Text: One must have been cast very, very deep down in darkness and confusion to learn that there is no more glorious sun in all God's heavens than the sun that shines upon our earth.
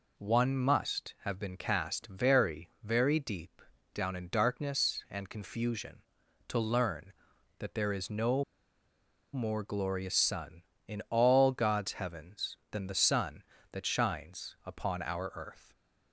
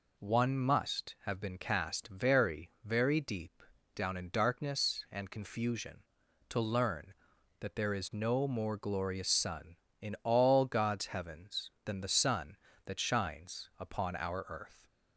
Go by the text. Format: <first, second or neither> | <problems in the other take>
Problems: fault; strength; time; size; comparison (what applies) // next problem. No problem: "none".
second | pauses between "deep" and "down"; slight; at 3.6 s; 0.30 s long; slight in the second // pauses between "no" and "more"; noticeable; at 8.4 s; 0.91 s long